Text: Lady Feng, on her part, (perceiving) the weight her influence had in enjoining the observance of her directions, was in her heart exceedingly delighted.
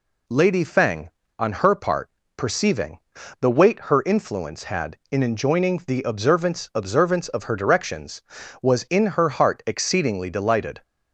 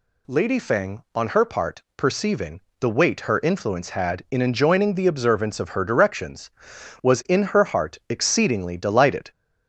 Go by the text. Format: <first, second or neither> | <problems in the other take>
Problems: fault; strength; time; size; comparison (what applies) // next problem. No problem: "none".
second | says "observance" twice; at 6.7 s